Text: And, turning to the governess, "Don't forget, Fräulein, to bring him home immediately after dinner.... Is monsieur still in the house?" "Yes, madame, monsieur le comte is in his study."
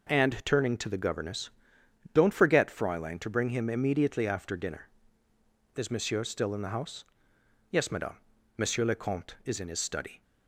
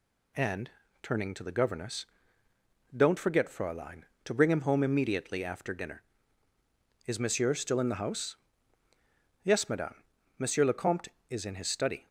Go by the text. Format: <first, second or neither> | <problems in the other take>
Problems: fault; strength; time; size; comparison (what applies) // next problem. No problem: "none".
second | skips "home"; at 3.6 s